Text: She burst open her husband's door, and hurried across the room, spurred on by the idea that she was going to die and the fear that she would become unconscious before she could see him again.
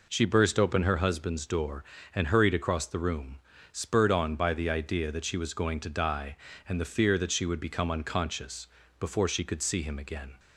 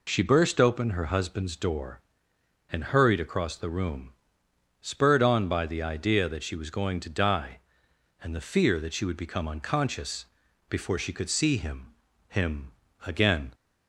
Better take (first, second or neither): first